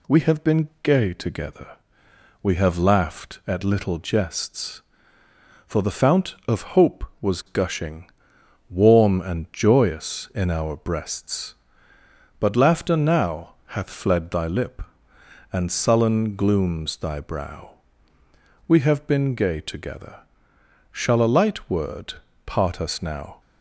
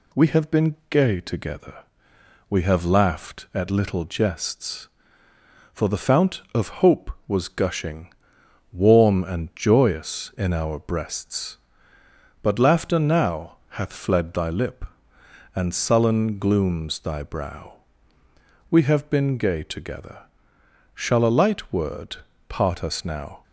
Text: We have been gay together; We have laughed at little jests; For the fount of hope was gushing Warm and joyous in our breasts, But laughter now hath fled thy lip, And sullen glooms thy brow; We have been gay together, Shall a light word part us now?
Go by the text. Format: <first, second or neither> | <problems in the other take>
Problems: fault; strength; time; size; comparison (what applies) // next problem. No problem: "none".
neither | pauses between "gushing" and "Warm"; noticeable; the same in both // pauses between "word" and "part"; slight; the same in both